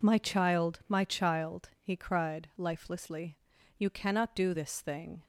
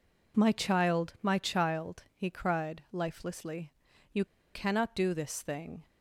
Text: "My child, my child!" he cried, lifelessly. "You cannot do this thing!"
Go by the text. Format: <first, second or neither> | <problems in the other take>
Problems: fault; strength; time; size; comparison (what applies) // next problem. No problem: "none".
first | pauses between "You" and "cannot"; slight; at 4.2 s; 0.27 s long